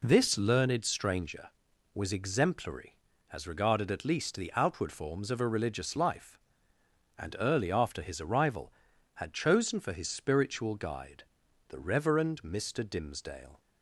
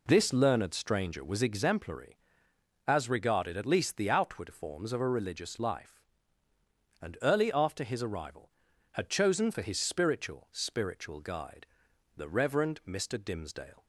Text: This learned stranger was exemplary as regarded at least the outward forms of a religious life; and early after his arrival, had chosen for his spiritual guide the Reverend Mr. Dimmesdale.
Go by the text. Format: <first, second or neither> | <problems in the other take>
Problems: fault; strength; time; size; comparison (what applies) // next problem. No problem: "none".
first | says "spiritual" twice; at 10.5 s // pauses between "guide" and "the"; noticeable; at 11.6 s; 0.54 s long; noticeable in the first